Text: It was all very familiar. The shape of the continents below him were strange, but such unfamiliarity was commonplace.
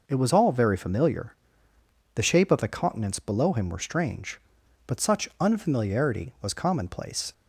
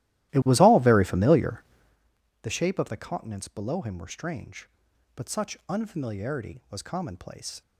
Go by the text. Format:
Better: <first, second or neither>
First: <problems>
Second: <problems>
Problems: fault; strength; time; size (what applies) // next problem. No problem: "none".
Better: first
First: none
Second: starts louder than the rest; strong; until 2.0 s; 15.5 dB